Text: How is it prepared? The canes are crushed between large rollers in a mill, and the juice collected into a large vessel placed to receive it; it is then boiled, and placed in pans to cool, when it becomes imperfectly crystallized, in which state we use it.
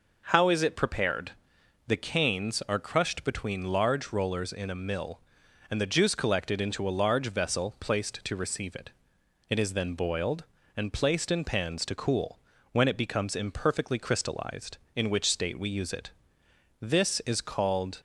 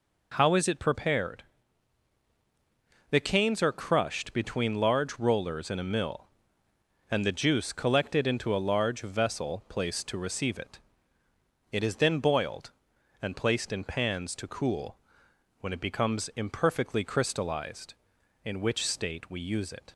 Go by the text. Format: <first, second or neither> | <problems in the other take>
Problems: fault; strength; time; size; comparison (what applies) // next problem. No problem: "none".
second | goes on to say "This is called"; noticeable; from 16.8 s on; 1.2 s long